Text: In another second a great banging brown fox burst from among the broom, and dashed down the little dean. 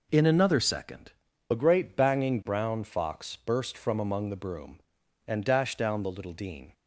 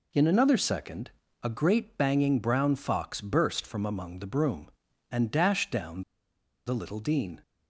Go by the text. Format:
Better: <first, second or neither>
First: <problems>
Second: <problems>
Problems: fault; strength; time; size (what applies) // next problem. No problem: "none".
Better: first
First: pauses between "second" and "a"; at 1.1 s; 0.38 s long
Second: pauses between "second" and "a"; slight; at 1.1 s; 0.30 s long // pauses between "down" and "the"; noticeable; at 6.0 s; 0.65 s long